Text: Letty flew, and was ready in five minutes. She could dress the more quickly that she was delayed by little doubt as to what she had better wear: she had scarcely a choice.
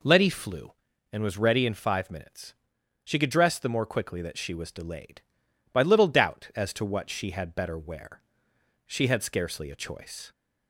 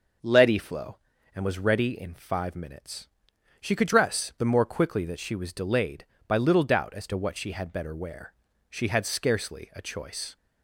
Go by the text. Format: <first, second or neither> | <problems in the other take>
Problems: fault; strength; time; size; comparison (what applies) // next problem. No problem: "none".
first | says "flow" for "flew"; at 0.5 s